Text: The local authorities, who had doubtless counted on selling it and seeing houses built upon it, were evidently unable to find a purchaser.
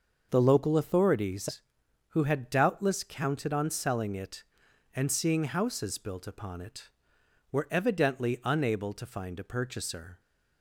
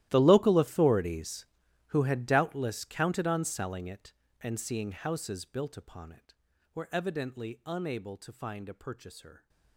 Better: first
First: starts louder than the rest; noticeable; until 1.3 s; 6 dB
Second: gets quieter; strong; throughout; 20.5 dB // starts louder than the rest; strong; until 1.1 s; 14 dB

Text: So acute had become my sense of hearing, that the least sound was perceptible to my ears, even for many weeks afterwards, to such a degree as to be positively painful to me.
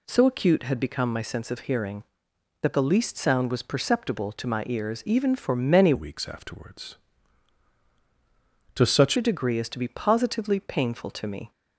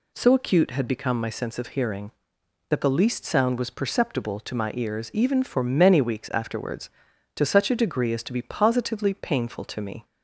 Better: second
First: changes voice from "weeks" to "such"; from 5.9 to 9.1 s; 3.2 s long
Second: none

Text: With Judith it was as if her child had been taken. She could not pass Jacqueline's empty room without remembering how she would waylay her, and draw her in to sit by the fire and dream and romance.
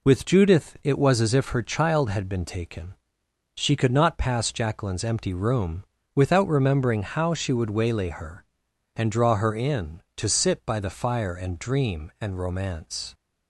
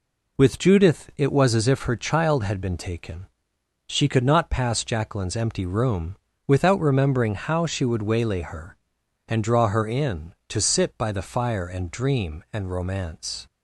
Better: neither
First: pauses between "room" and "without"; slight; at 5.8 s; 0.32 s long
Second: pauses between "room" and "without"; slight; at 6.1 s; 0.32 s long

